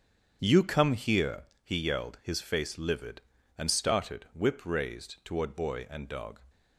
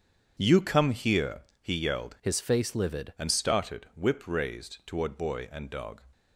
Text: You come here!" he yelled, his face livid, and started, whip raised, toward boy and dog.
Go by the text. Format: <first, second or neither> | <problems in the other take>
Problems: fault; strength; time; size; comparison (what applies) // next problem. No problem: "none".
first | starts louder than the rest; strong; until 1.3 s; 8 dB; strong in the first // changes voice from "his" to "livid"; from 2.2 to 3.1 s; 0.9 s long